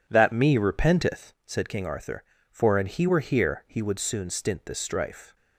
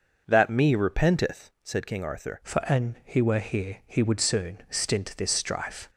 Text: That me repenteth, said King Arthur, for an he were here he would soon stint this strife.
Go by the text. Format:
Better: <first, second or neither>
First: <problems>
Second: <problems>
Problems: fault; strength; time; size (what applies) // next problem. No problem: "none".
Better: first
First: none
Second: changes voice at "for"; from 2.4 s on; 3.4 s long